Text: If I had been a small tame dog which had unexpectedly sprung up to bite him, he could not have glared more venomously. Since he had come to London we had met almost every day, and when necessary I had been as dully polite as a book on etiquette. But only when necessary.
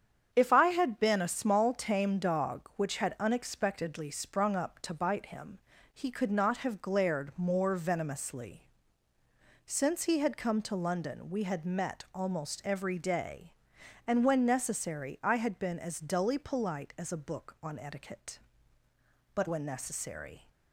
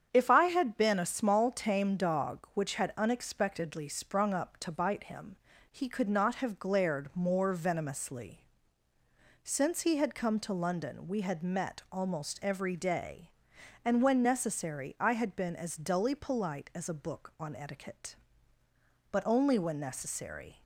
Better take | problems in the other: second | starts louder than the rest; strong; until 1.3 s; 8 dB; strong in the second // skips "only"; at 19.4 s

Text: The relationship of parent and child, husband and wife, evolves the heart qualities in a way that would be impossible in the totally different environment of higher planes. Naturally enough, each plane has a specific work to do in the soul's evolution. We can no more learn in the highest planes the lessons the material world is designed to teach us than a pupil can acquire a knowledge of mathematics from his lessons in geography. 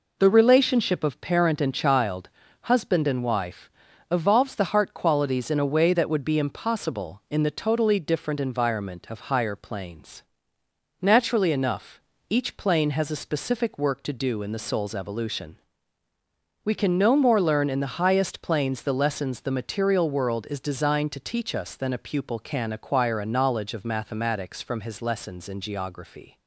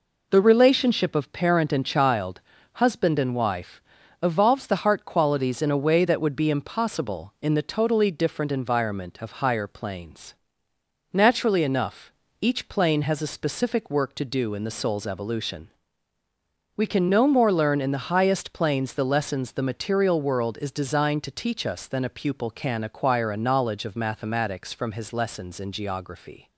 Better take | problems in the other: neither | none

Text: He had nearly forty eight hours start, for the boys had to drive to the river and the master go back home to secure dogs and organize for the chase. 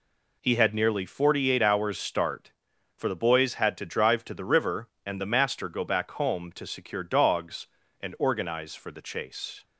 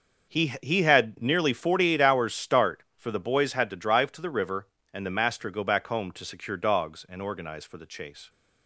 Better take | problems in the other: first | says "He" twice; at 0.6 s

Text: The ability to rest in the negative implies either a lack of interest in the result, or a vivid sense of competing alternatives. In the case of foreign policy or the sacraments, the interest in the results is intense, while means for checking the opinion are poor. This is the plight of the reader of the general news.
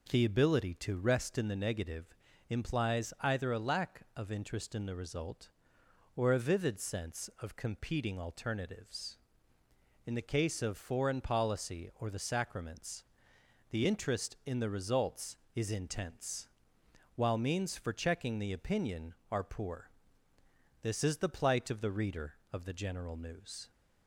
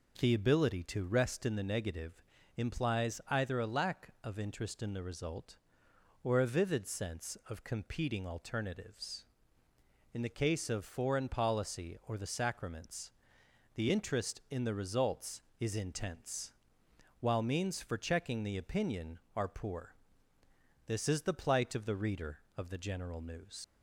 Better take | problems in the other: first | pauses between "negative" and "implies"; slight; at 2.2 s; 0.32 s long; slight in the first // leaves "news" unfinished; at 23.6 s; 105 ms

